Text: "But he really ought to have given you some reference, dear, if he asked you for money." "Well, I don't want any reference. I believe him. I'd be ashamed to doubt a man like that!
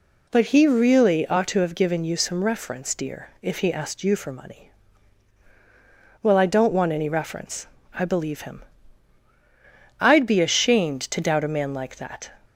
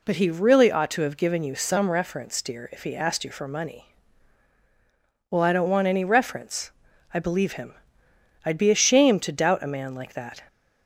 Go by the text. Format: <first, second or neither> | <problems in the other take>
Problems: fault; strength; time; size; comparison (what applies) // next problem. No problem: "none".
neither | none